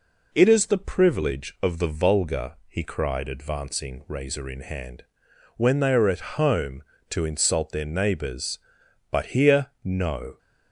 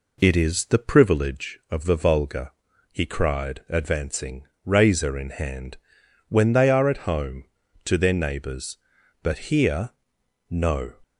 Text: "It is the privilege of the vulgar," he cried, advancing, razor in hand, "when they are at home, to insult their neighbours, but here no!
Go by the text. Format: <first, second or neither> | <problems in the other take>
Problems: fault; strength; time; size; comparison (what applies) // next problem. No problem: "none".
first | skips "insult"; at 7.9 s // pauses between "here" and "no"; noticeable; at 9.9 s; 0.58 s long; slight in the first